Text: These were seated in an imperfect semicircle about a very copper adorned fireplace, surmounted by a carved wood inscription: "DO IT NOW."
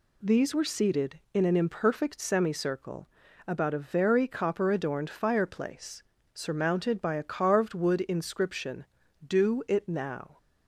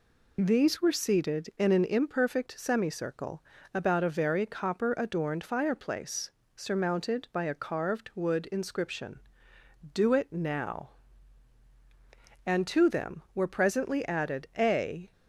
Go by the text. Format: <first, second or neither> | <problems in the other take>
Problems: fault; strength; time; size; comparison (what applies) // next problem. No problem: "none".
first | pauses between "semicircle" and "about"; slight; at 3.4 s; 0.30 s long; also in the first // goes on to say "And to them were presently added a"; strong; from 12.4 s on; 2.6 s long